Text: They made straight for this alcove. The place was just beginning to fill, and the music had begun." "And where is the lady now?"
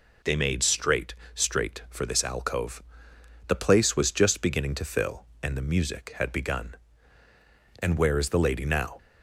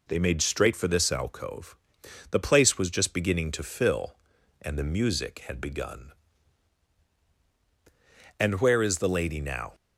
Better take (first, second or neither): second